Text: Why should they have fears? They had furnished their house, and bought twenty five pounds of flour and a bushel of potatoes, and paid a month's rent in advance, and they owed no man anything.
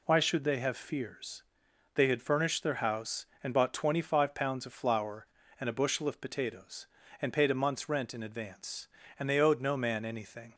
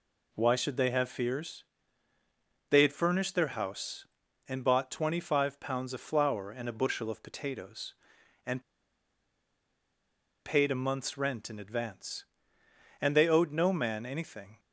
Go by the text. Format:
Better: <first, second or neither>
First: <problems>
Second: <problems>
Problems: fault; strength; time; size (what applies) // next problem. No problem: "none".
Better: first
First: none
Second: pauses between "and" and "paid"; strong; at 8.6 s; 1.8 s long